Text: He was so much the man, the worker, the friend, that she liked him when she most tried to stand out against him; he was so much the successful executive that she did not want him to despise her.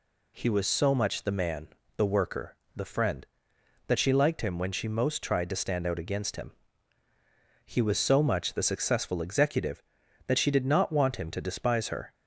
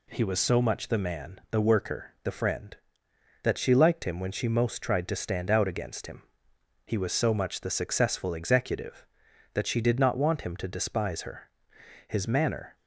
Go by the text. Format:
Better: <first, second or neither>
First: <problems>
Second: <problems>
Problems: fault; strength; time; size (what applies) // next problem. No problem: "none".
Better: first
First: none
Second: goes on to say "His manner"; noticeable; from 12.0 s on; 0.68 s long